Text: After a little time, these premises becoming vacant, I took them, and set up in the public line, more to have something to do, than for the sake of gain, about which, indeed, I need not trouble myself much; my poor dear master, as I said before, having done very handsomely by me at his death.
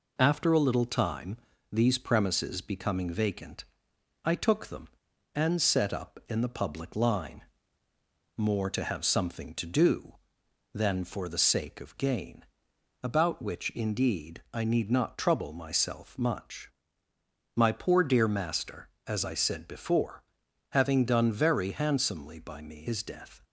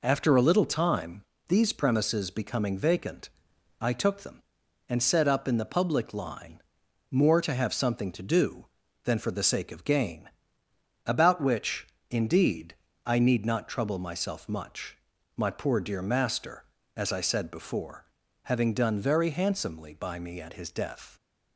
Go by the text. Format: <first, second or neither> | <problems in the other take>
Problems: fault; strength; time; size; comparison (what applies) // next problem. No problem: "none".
second | skips "at"; at 22.8 s